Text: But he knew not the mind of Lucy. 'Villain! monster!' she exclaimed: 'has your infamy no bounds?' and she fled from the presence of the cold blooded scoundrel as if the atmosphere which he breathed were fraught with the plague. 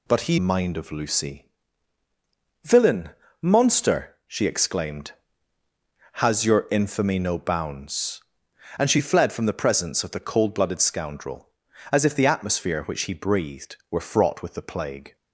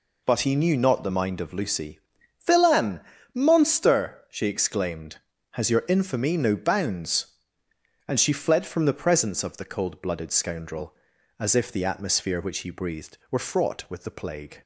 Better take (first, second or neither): second